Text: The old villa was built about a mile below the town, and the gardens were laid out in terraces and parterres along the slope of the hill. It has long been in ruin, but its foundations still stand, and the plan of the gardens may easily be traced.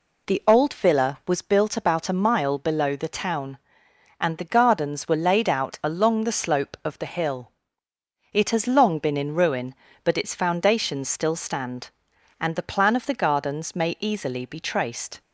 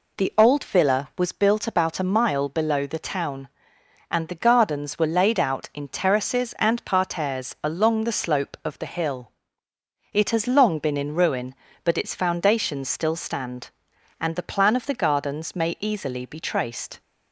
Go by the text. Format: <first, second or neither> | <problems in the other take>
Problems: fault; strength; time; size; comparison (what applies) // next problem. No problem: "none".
second | skips "in terraces and parterres"; at 5.7 s